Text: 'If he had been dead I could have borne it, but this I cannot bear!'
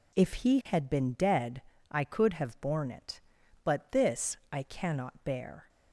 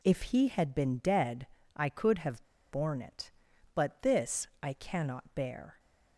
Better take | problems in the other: first | pauses between "dead" and "I"; slight; at 1.4 s; 0.30 s long; slight in the first // pauses between "have" and "borne"; slight; at 2.4 s; 0.27 s long

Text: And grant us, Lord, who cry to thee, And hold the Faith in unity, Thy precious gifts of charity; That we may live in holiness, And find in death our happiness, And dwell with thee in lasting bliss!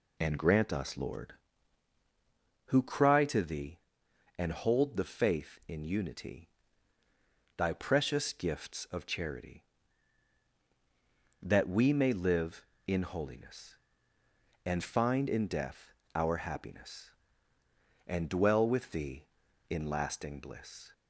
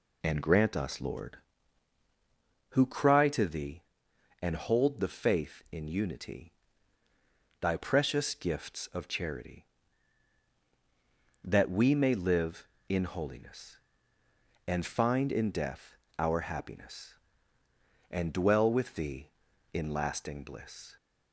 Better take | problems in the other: neither | pauses between "death" and "our"; slight; the same in both

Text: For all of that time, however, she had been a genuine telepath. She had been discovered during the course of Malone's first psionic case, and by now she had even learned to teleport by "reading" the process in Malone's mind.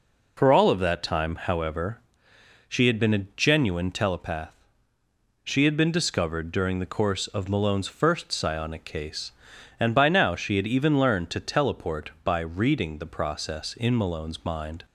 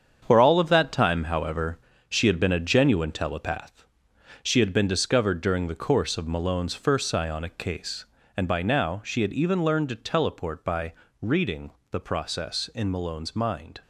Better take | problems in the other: first | gets quieter; strong; throughout; 8.5 dB // pauses between "by" and "reading"; slight; at 10.9 s; 0.28 s long // pauses between "reading" and "the"; slight; at 11.7 s; 0.20 s long

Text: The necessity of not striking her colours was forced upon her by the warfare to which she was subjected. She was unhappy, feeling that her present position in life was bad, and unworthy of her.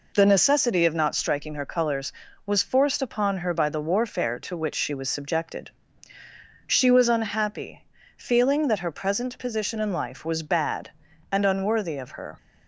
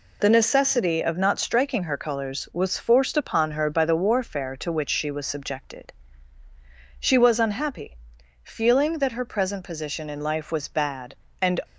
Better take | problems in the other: first | stops before "unworthy of her"; at 11.6 s

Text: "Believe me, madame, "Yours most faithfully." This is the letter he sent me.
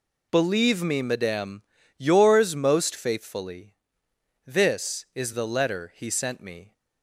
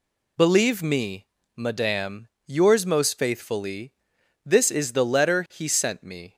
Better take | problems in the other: neither | none

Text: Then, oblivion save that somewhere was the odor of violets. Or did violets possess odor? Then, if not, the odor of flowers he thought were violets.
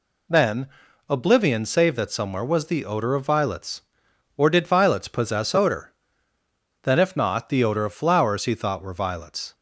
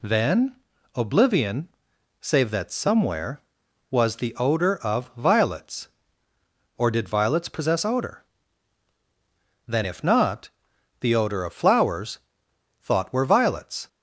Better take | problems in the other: first | pauses between "oblivion" and "save"; noticeable; at 1.6 s; 0.50 s long // skips "he"; at 12.4 s

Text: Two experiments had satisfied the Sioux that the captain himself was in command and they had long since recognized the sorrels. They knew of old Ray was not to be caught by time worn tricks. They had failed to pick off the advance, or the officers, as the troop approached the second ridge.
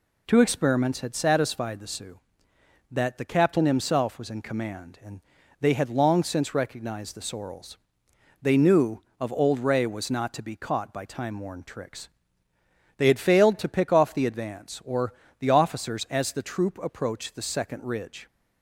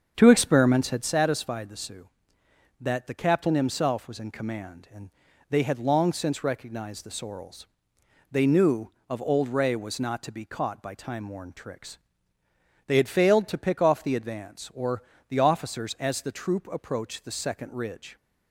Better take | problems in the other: first | starts louder than the rest; strong; until 1.1 s; 7 dB // pauses between "and" and "they"; at 5.1 s; 0.38 s long; also in the first // pauses between "or" and "the"; slight; at 15.0 s; 0.26 s long; slight in the first

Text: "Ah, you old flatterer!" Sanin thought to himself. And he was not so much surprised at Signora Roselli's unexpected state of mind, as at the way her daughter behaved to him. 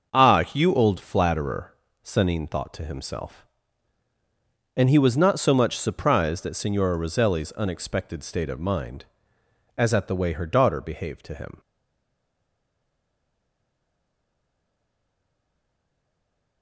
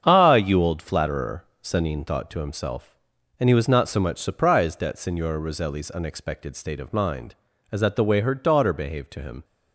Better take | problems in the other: second | starts louder than the rest; until 1.2 s; 7 dB; strong in the second // stays silent after the last word; strong; from 11.5 s on; 5.1 s long

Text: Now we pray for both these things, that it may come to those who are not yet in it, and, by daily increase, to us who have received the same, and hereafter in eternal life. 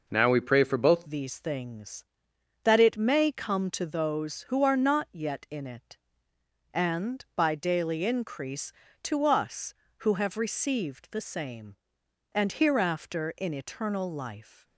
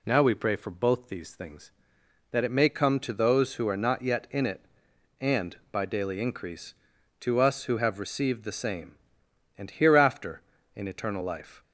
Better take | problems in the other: second | changes voice at "these"; from 1.0 s on; 13.6 s long

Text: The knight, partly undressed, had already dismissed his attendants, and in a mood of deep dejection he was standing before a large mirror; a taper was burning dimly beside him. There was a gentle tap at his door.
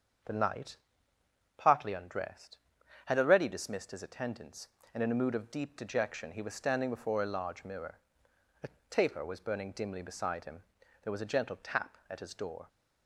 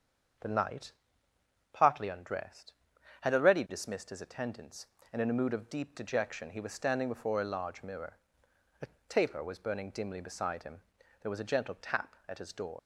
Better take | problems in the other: first | starts louder than the rest; strong; until 2.2 s; 7 dB; strong in the first // pauses between "a" and "taper"; slight; at 8.8 s; 0.22 s long; slight in the first // leaves "door" unfinished; at 12.7 s; 70 ms

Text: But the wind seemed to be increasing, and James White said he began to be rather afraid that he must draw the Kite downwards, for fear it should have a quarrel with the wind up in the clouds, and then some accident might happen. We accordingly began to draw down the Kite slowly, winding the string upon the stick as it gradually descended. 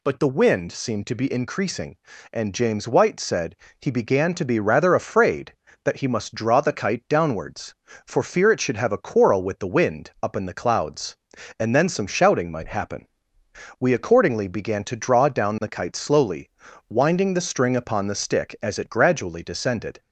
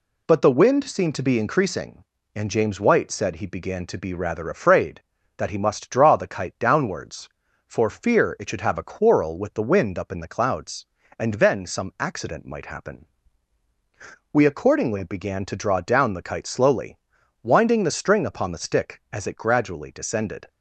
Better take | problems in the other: second | pauses between "said" and "he"; slight; at 3.5 s; 0.24 s long // says "shouting" for "accident"; at 12.0 s

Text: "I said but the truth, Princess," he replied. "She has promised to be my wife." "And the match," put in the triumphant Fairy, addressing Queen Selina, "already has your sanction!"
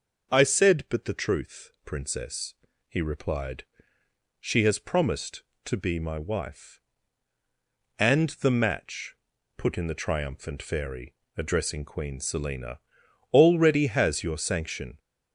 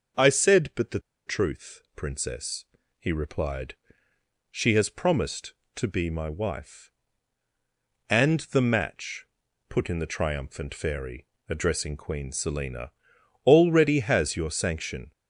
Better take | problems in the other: first | starts louder than the rest; until 1.4 s; 6 dB; noticeable in the first // pauses between "the" and "truth"; slight; at 1.0 s; 0.25 s long

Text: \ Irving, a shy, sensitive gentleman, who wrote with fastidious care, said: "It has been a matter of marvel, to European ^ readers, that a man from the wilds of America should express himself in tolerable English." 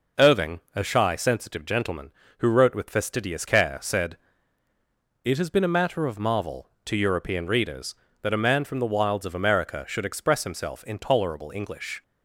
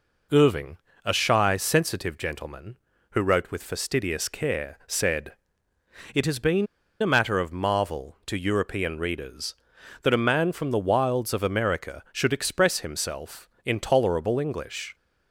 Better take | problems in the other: first | pauses between "been" and "a"; slight; at 6.6 s; 0.34 s long

